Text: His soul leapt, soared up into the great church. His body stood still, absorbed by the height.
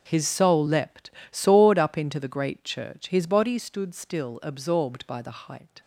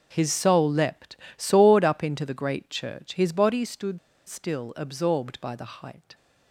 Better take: first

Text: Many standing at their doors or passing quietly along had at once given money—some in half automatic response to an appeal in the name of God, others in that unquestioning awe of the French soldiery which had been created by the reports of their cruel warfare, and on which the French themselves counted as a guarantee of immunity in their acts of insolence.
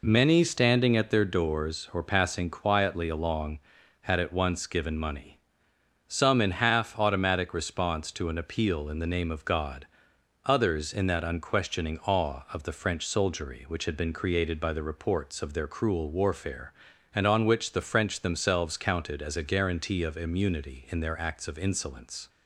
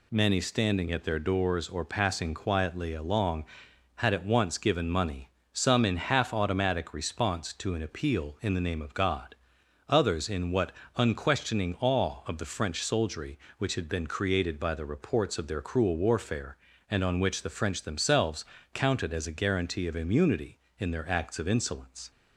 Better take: first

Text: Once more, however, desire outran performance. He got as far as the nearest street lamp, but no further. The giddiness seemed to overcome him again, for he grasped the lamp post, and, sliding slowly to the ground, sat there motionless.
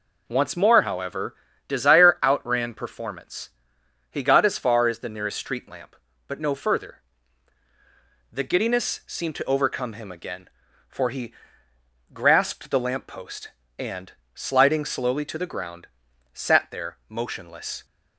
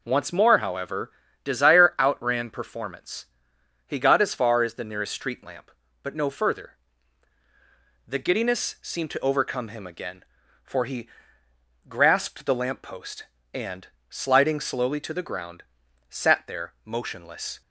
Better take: neither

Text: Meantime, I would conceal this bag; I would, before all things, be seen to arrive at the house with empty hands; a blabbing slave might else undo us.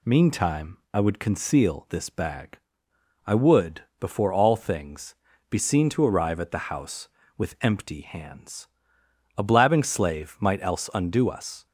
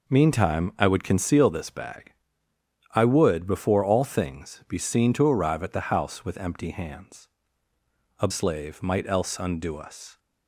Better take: first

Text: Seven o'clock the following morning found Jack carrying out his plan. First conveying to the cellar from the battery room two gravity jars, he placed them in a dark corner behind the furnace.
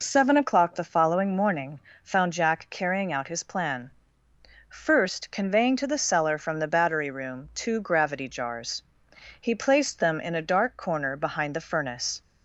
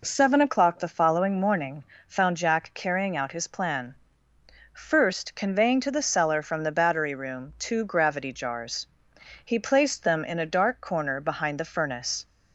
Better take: second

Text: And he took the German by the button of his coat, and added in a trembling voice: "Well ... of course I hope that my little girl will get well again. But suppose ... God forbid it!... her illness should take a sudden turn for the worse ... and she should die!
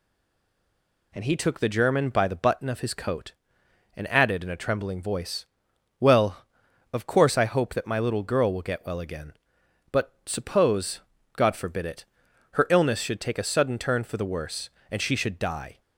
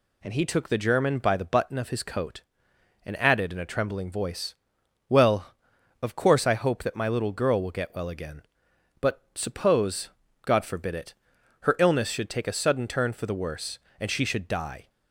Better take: second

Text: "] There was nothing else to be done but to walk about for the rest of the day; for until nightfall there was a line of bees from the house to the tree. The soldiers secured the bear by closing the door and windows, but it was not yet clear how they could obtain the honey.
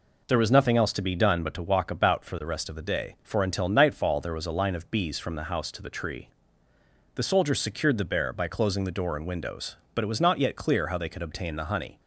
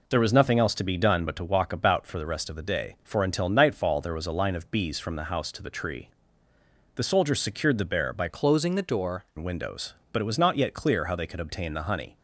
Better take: first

